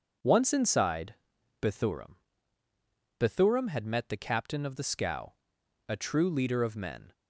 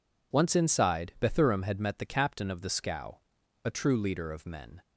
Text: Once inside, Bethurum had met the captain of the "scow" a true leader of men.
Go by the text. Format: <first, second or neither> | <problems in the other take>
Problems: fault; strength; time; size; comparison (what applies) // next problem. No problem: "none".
second | says "Bethurum" twice; at 3.1 s // pauses between "scow" and "a"; noticeable; at 5.3 s; 0.52 s long; noticeable in the second